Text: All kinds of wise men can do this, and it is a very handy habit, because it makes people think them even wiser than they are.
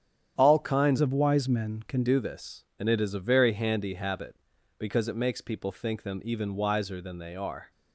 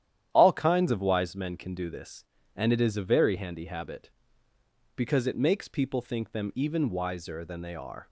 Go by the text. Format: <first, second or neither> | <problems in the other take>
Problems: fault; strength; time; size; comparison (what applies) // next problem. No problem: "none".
second | starts louder than the rest; strong; until 1.4 s; 9 dB; strong in the second // changes voice from "of" to "can"; from 1.0 to 2.0 s; 1.0 s long